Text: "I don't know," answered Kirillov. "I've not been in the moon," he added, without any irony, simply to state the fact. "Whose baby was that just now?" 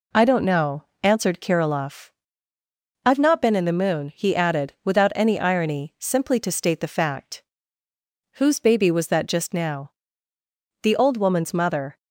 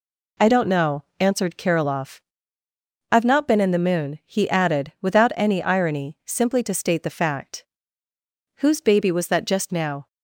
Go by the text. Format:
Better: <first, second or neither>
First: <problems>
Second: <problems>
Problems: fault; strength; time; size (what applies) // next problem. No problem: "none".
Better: second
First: goes on to say "The old woman's mother"; noticeable; from 10.8 s on; 1.1 s long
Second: none